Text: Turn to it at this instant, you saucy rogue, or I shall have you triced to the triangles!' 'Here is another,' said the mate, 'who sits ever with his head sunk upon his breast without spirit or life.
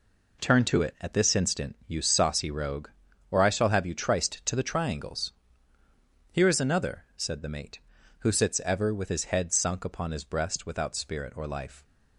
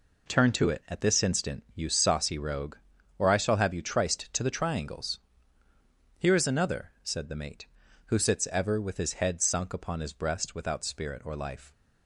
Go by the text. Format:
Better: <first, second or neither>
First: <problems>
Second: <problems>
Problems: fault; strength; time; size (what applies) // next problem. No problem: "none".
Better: neither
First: none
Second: none